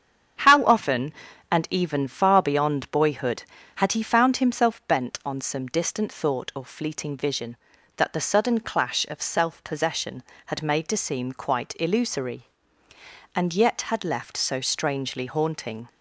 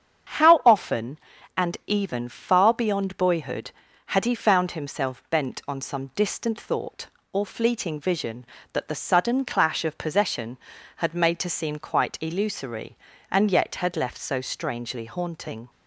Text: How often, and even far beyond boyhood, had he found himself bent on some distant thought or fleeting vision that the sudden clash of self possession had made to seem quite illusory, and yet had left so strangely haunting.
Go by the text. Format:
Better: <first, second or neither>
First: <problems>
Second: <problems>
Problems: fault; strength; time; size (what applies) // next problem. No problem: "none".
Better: first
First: starts louder than the rest; strong; until 1.8 s; 8.5 dB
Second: starts louder than the rest; strong; until 1.7 s; 8 dB // skips "self"; at 9.9 s